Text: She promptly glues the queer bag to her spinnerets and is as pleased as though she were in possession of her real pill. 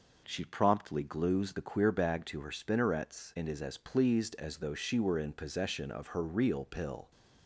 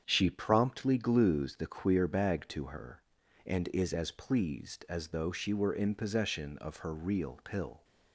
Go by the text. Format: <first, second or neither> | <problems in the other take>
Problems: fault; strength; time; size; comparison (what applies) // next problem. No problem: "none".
first | starts louder than the rest; strong; until 1.0 s; 8 dB // skips "spinnerets"; at 3.2 s